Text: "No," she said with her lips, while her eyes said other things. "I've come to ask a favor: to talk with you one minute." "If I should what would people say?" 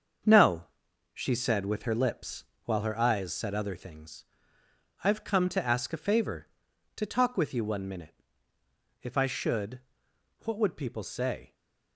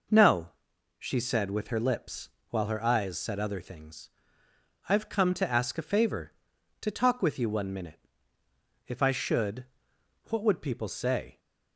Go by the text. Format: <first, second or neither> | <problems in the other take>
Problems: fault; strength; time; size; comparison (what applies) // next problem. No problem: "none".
second | gets quieter; strong; throughout; 7.5 dB // pauses between "should" and "what"; noticeable; at 9.7 s; 0.64 s long; noticeable in the second // stays silent after the last word; slight; from 11.4 s on; 0.5 s long